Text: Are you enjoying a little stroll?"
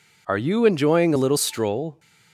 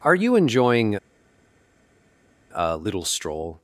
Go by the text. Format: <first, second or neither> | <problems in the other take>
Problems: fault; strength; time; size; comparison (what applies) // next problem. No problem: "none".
first | pauses between "enjoying" and "a"; strong; at 0.9 s; 1.5 s long